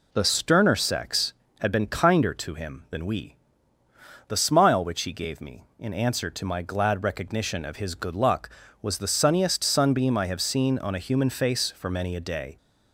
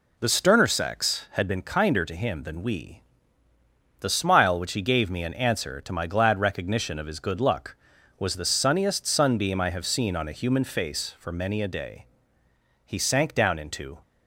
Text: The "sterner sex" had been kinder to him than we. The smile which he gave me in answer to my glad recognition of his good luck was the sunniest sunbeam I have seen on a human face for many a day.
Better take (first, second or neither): first